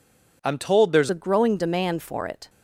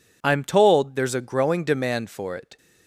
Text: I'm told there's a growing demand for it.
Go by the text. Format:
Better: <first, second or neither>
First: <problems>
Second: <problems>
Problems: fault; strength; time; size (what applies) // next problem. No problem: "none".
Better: second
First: changes voice at "a"; from 1.1 s on; 1.3 s long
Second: none